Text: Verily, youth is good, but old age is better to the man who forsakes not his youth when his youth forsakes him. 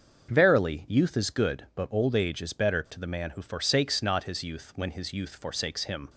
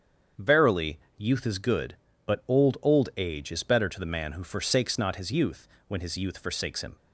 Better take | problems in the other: first | starts louder than the rest; strong; until 1.5 s; 7.5 dB; also in the first // says "old" twice; at 2.8 s // pauses between "youth" and "when"; slight; at 5.6 s; 0.18 s long

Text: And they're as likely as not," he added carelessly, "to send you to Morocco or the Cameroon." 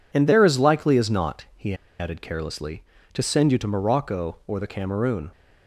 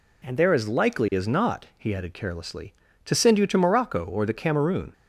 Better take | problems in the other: second | pauses between "he" and "added"; slight; at 1.7 s; 0.25 s long

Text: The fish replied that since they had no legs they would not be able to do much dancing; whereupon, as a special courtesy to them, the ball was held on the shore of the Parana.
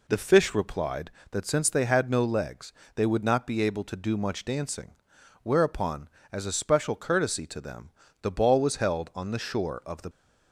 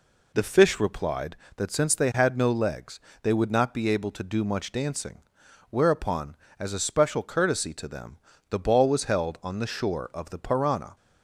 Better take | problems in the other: second | pauses between "legs" and "they"; slight; at 2.7 s; 0.24 s long; slight in the second // stops before "Parana"; at 10.1 s

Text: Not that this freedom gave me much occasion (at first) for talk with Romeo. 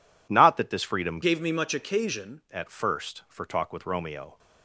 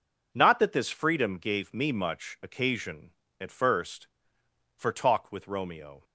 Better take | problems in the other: second | changes voice from "gave" to "occasion"; from 1.2 to 2.4 s; 1.2 s long

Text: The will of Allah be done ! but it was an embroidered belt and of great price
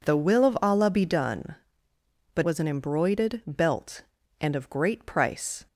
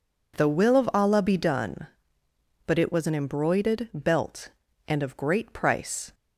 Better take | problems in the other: second | skips "it"; at 2.4 s

